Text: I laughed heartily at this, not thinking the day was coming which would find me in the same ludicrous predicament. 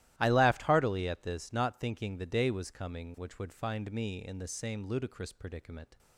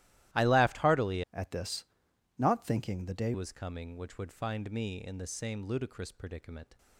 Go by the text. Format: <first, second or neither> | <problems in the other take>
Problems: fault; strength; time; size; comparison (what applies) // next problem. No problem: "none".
first | starts louder than the rest; strong; until 1.4 s; 15 dB; strong in the first // changes voice from "at" to "day"; from 1.3 to 3.3 s; 2.0 s long